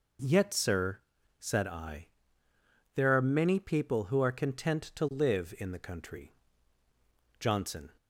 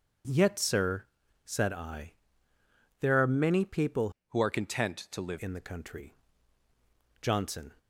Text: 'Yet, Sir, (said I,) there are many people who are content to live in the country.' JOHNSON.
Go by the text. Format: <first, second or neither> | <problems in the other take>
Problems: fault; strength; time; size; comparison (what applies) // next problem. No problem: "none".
first | changes voice from "who" to "live"; from 4.2 to 5.3 s; 1.1 s long